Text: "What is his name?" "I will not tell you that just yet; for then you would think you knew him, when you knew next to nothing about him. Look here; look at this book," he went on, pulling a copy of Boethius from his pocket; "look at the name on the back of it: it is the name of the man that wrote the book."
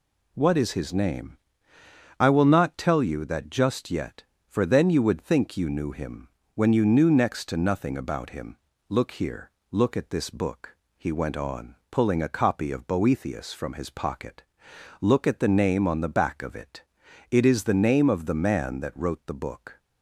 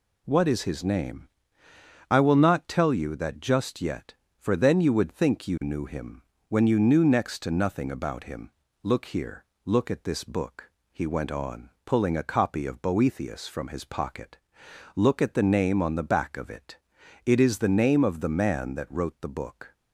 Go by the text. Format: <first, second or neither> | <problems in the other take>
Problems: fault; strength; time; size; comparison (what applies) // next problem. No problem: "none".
neither | none